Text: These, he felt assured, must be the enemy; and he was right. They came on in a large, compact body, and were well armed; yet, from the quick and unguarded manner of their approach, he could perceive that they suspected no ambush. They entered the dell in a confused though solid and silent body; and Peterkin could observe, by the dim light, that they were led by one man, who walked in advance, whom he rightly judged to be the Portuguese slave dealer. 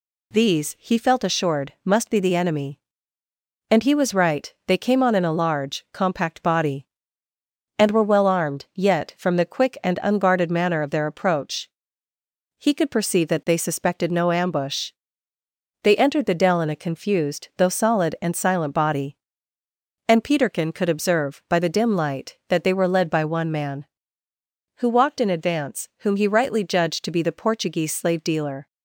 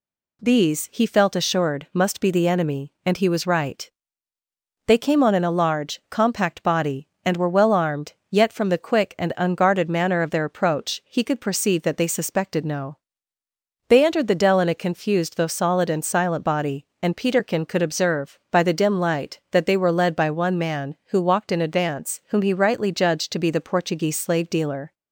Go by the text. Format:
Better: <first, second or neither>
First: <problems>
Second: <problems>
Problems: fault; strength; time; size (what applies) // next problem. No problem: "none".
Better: first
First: none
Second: skips "ambush"; at 13.4 s